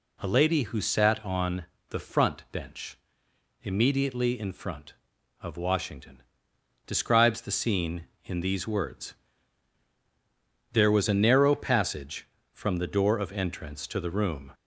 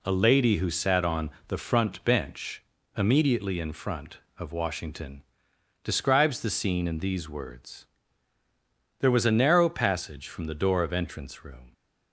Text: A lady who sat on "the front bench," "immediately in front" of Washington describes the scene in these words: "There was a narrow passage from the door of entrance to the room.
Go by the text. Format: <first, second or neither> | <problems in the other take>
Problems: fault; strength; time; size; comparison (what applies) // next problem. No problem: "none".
first | pauses between "on" and "the"; slight; at 1.2 s; 0.20 s long; slight in the first // pauses between "Washington" and "describes"; noticeable; at 5.2 s; 0.62 s long; noticeable in the first // skips "to the"; at 11.4 s